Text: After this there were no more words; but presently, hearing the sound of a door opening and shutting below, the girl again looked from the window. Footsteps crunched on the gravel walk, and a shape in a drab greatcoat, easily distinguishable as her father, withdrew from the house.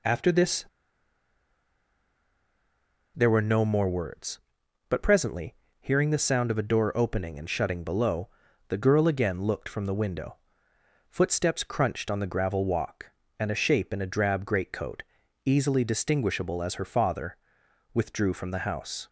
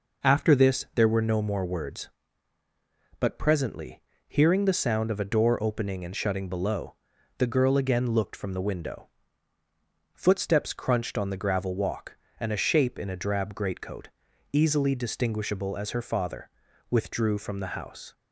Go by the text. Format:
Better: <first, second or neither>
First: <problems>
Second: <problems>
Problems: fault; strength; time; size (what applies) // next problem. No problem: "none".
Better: second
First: pauses between "this" and "there"; strong; at 0.6 s; 2.5 s long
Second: none